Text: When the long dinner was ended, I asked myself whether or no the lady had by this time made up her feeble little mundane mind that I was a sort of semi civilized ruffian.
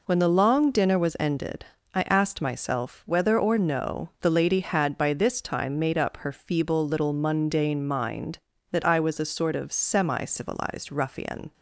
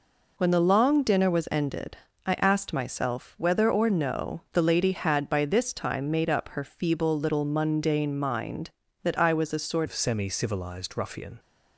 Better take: first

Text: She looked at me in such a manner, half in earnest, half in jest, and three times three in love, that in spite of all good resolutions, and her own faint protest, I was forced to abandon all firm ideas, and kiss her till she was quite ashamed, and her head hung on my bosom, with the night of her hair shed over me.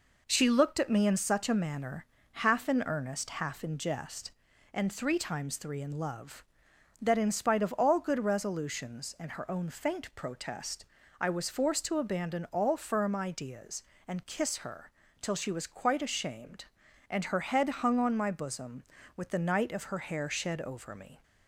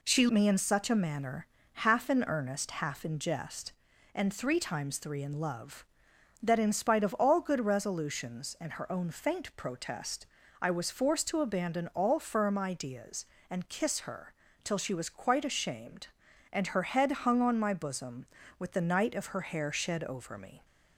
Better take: first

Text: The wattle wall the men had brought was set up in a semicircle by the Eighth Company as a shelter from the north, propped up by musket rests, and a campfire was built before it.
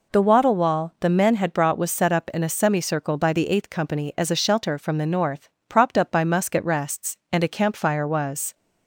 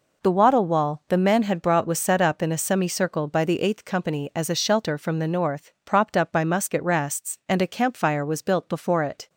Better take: second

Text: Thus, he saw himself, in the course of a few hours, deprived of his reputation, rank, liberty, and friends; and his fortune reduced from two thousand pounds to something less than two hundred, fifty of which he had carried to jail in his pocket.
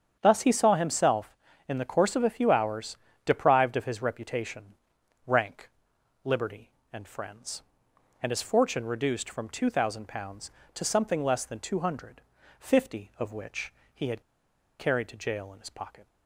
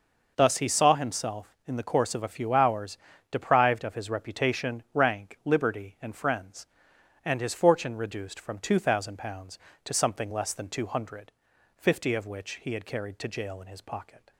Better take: second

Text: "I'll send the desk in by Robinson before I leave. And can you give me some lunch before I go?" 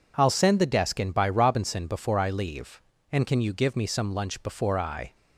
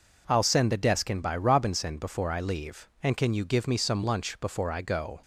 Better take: second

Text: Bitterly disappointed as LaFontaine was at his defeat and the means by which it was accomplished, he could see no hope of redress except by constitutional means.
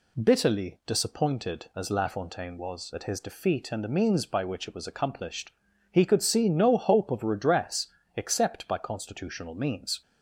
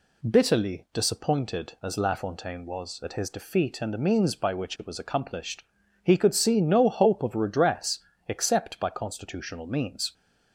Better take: neither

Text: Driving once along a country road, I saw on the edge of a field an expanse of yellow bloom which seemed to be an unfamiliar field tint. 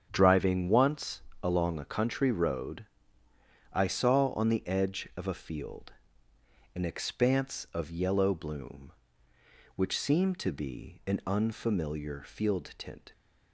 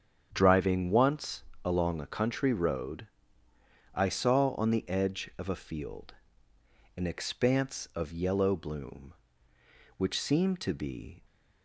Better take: first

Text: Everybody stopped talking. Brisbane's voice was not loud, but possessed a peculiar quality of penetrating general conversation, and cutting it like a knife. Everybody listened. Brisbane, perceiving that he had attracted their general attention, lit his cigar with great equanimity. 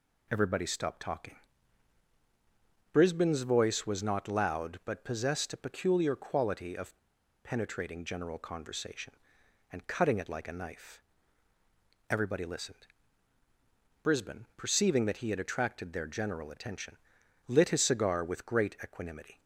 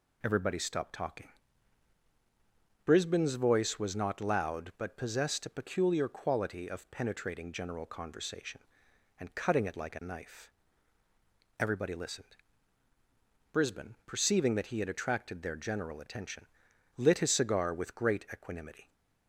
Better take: second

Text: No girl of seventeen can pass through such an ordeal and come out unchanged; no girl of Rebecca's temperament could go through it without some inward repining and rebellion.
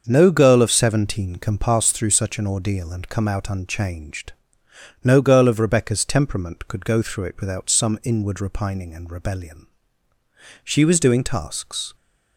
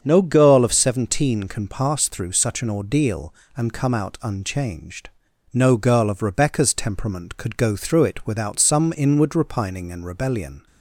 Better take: second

